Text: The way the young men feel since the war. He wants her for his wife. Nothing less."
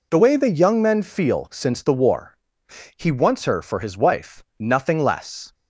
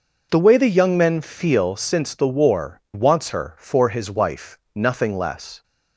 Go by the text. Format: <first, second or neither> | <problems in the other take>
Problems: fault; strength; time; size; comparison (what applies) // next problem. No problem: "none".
first | skips "He"; at 2.8 s